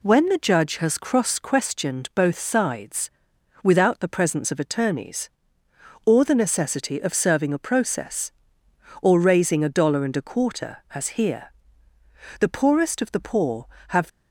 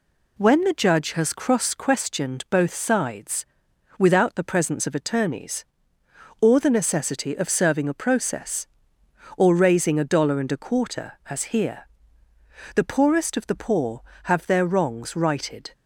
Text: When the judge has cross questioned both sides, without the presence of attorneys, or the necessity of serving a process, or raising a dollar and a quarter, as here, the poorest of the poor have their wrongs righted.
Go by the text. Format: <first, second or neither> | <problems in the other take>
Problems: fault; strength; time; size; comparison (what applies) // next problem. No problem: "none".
second | stops before "their wrongs righted"; at 14.0 s